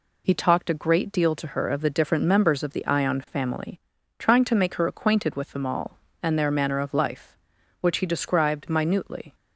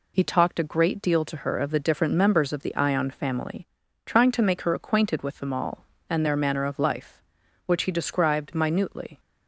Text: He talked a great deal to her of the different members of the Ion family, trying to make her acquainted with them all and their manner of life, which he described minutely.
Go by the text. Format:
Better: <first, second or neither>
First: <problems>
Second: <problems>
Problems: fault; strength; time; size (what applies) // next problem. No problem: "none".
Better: neither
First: none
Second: none